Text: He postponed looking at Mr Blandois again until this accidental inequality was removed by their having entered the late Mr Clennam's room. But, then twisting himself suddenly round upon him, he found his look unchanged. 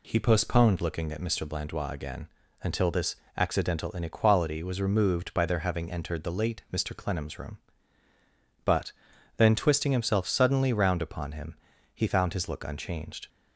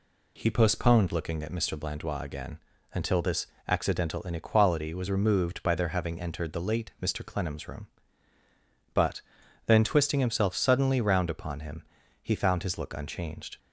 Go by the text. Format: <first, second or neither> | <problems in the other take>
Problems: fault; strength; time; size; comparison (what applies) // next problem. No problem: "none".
neither | pauses between "again" and "until"; slight; the same in both // pauses between "this" and "accidental"; slight; the same in both